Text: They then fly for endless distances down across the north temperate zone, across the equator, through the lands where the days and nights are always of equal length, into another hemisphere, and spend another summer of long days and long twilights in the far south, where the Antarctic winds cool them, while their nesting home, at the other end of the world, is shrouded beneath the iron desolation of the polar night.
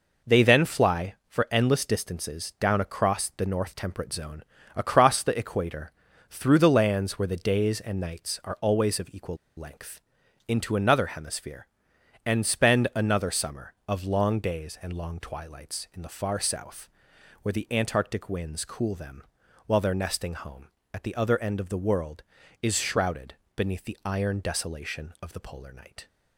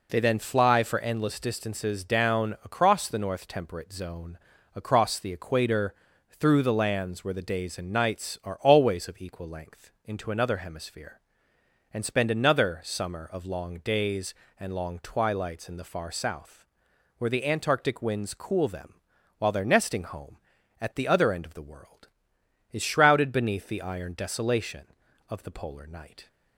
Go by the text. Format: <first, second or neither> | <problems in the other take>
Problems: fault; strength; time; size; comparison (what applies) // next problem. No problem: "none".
second | pauses between "equal" and "length"; slight; at 9.3 s; 0.20 s long // pauses between "shrouded" and "beneath"; slight; at 23.3 s; 0.20 s long